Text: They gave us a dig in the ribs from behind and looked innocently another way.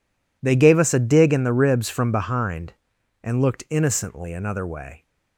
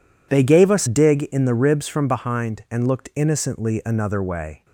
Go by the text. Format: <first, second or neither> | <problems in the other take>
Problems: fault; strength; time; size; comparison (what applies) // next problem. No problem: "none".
first | skips "a"; at 0.8 s